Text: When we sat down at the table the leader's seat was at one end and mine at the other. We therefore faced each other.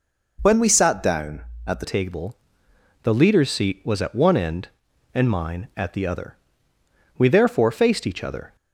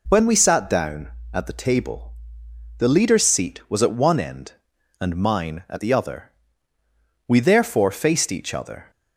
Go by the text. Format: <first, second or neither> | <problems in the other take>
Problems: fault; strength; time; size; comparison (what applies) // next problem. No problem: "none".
second | changes voice at "table"; from 1.8 s on; 6.7 s long // pauses between "table" and "the"; noticeable; at 2.3 s; 0.68 s long; noticeable in the second